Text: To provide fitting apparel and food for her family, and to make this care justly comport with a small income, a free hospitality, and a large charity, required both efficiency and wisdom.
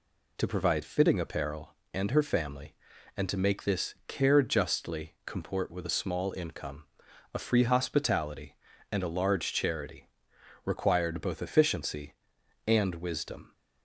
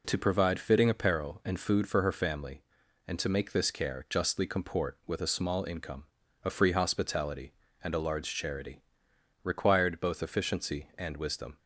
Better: second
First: skips "food for"; at 2.0 s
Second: none

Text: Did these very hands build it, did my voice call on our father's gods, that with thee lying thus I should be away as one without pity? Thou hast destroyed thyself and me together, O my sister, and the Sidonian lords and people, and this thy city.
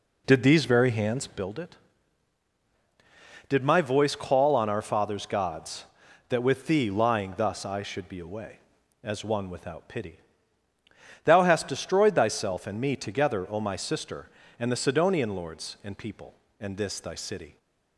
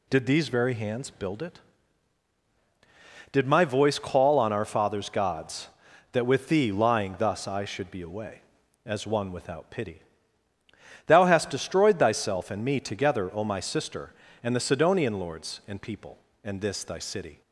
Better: second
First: starts louder than the rest; slight; until 1.5 s; 3 dB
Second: none

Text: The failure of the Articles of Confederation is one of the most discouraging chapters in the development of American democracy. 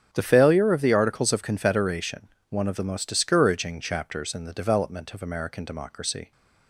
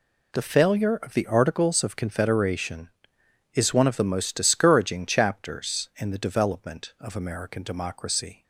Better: second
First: starts louder than the rest; strong; until 1.1 s; 8 dB // skips "is"; at 2.3 s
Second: none

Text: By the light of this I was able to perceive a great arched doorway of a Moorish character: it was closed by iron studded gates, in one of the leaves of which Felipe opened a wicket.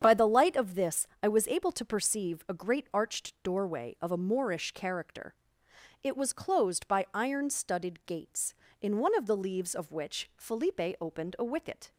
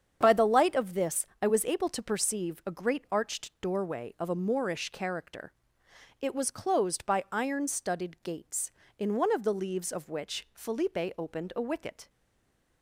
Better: first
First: starts louder than the rest; strong; until 1.0 s; 8 dB // pauses between "this" and "I"; slight; at 1.0 s; 0.16 s long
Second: starts louder than the rest; strong; until 1.2 s; 8 dB // pauses between "this" and "I"; slight; at 1.2 s; 0.16 s long // stays silent after the last word; slight; from 12.0 s on; 0.8 s long

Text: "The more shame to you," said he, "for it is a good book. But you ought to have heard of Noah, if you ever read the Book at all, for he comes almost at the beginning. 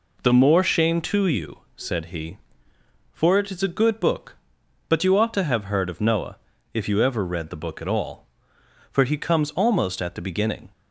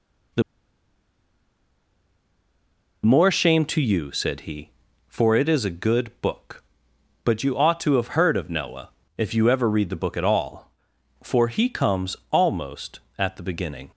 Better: first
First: none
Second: pauses between "The" and "more"; strong; at 0.4 s; 2.6 s long // pauses between "comes" and "almost"; slight; at 12.1 s; 0.16 s long

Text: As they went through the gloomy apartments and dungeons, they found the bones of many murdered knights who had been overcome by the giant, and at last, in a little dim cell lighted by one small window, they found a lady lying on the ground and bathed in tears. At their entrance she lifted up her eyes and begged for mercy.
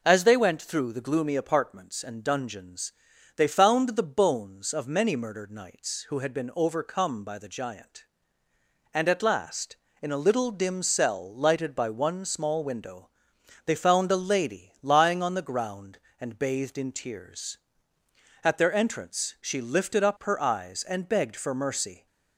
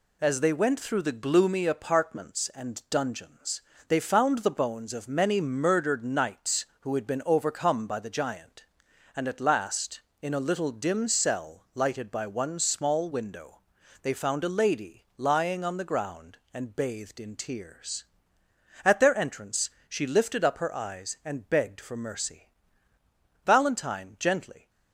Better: first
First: none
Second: pauses between "entrance" and "she"; slight; at 19.6 s; 0.20 s long // goes on to say "Valentine gently"; noticeable; from 23.4 s on; 1.2 s long

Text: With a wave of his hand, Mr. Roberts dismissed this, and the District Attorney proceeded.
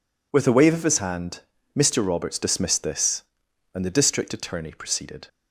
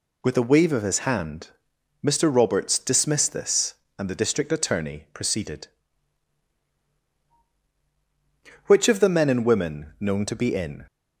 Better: first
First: none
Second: goes on to say "Which of the men and women known to be in"; strong; from 8.6 s on; 2.2 s long

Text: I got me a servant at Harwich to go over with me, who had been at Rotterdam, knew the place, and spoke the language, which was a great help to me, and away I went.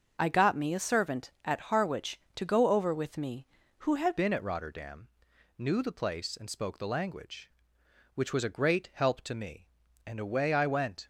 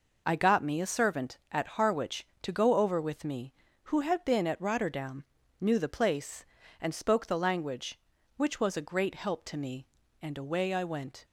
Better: second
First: starts louder than the rest; until 1.1 s; 6.5 dB // changes voice at "been"; from 4.1 s on; 6.9 s long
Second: none

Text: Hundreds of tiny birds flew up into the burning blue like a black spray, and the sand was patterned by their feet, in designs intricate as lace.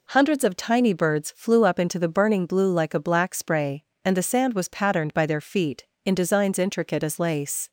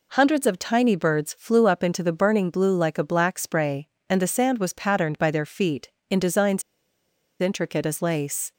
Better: first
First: none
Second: pauses between "designs" and "intricate"; noticeable; at 6.6 s; 0.78 s long

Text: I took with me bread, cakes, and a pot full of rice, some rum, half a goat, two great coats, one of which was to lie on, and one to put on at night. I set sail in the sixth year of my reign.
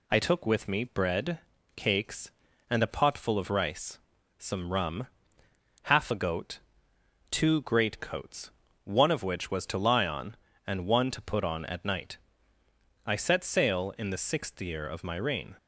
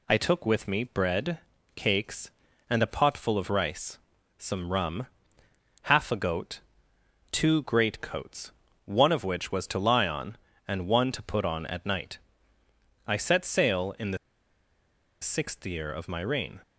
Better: first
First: none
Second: pauses between "the" and "sixth"; at 14.1 s; 1.0 s long

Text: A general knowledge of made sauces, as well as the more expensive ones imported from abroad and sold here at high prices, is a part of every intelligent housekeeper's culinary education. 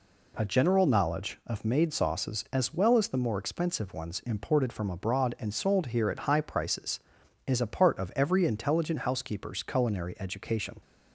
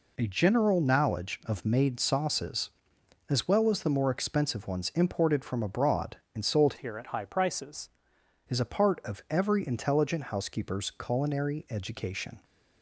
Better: first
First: none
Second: changes voice from "here" to "prices"; from 6.7 to 7.8 s; 1.1 s long

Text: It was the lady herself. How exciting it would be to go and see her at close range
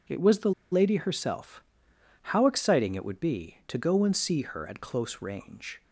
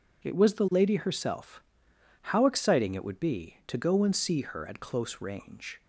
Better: second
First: pauses between "the" and "lady"; slight; at 0.5 s; 0.19 s long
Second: none

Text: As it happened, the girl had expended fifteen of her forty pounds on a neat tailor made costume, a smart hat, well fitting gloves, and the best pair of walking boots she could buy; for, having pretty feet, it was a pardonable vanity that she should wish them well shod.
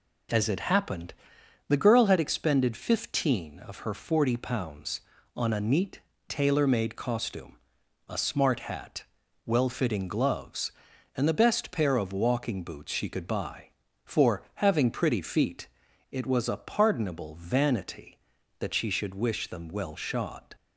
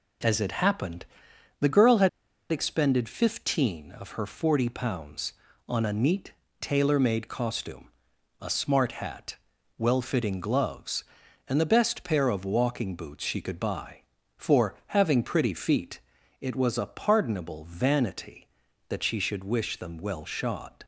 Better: first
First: pauses between "neat" and "tailor"; slight; at 6.0 s; 0.28 s long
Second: pauses between "had" and "expended"; at 2.0 s; 0.42 s long // pauses between "neat" and "tailor"; slight; at 6.3 s; 0.28 s long

